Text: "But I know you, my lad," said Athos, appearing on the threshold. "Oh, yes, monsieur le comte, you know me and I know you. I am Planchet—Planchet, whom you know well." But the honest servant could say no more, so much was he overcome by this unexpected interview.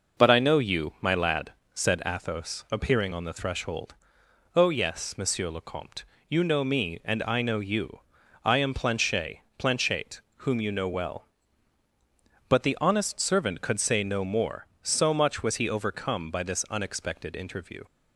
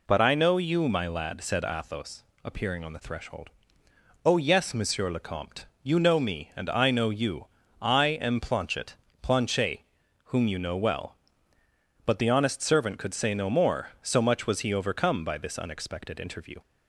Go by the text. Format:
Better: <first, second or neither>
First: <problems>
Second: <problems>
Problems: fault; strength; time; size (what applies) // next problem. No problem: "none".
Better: neither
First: none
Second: none